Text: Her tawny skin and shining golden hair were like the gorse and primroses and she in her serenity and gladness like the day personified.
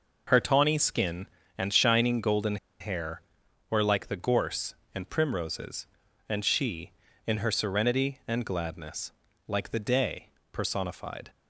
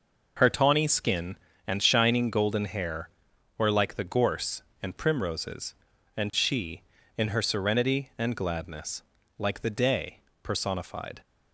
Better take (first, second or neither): second